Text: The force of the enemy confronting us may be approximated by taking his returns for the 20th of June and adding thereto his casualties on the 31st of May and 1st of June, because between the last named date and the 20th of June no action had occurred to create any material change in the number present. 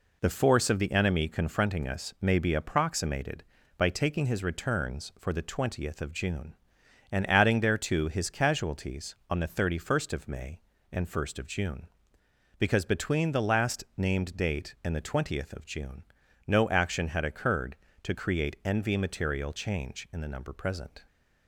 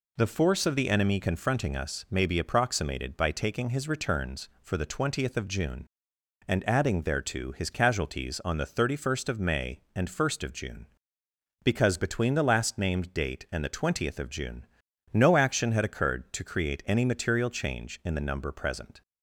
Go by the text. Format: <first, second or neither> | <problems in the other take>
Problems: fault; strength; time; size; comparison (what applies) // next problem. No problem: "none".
second | pauses between "June" and "no"; at 16.0 s; 0.44 s long; noticeable in the second // says "envy" for "any"; at 18.6 s